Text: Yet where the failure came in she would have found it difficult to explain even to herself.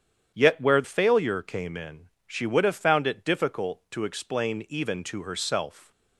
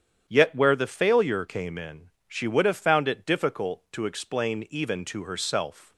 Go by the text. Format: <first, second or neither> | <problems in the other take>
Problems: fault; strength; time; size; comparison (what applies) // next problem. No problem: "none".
second | starts louder than the rest; strong; until 1.3 s; 9 dB; strong in the second // skips "the"; at 0.8 s // pauses between "in" and "she"; slight; at 2.0 s; 0.18 s long; slight in the second